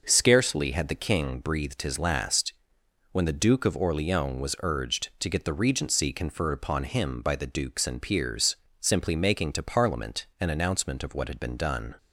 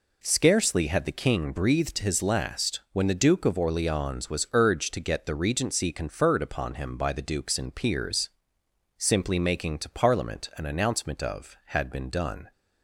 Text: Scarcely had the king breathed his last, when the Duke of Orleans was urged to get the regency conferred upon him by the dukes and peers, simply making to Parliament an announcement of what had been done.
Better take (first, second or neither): first